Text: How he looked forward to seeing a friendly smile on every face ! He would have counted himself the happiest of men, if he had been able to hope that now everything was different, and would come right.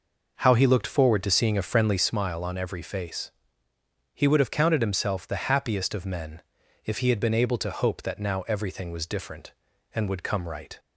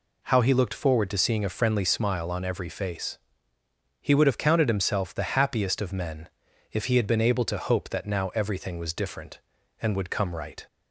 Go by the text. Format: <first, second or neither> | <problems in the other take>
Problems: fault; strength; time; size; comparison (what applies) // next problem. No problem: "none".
second | starts louder than the rest; noticeable; until 2.2 s; 5.5 dB